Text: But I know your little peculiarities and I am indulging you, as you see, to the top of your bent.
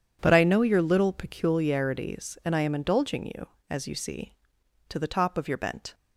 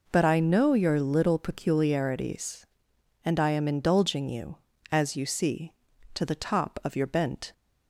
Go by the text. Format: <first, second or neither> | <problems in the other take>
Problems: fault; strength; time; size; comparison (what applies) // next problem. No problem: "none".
neither | none